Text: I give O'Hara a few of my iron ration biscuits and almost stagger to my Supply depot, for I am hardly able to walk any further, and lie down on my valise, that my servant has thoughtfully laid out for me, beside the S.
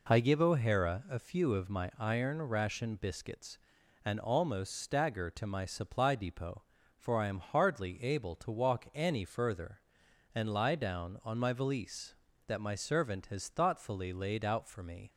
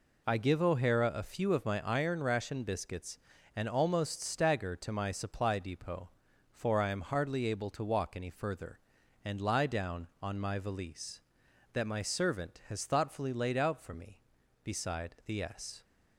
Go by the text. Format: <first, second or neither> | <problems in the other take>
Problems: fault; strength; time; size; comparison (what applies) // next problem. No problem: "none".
second | stops before "beside the S"; at 15.0 s